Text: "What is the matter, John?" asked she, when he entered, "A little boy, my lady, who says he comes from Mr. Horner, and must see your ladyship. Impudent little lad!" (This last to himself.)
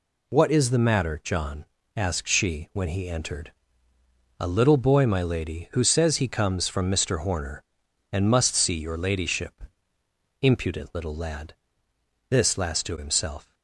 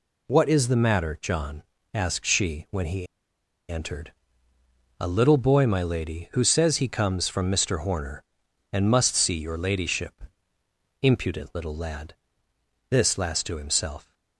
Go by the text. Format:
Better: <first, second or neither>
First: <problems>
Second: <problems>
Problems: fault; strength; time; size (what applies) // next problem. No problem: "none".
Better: first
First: none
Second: pauses between "he" and "entered"; noticeable; at 3.0 s; 0.64 s long